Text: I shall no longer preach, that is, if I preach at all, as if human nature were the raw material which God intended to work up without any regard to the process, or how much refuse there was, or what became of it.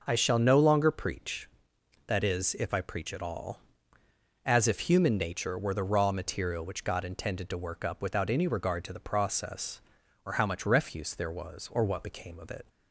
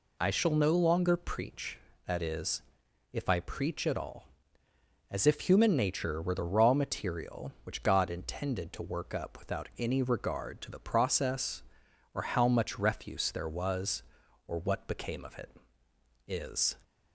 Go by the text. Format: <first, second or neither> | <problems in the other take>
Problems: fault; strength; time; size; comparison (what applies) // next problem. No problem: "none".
first | goes on to say "Is"; slight; from 16.2 s on; 0.48 s long